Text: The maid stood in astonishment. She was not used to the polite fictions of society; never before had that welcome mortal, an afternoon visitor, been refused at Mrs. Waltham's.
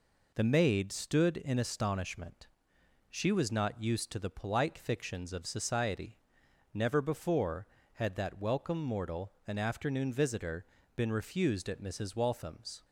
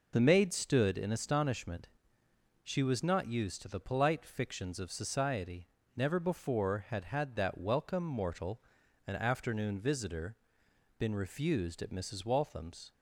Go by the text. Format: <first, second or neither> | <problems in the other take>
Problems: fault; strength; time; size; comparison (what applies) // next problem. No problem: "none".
first | says "had" twice; at 7.0 s